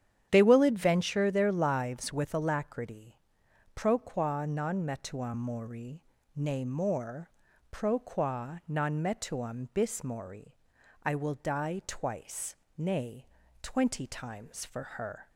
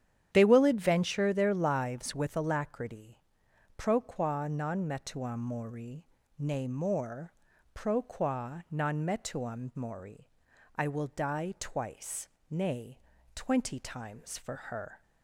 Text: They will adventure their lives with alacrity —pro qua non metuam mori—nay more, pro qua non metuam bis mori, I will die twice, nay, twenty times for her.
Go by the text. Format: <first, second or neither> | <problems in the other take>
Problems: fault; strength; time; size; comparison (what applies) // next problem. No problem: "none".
first | starts louder than the rest; strong; until 1.3 s; 9.5 dB; strong in the first // skips "bis"; at 9.7 s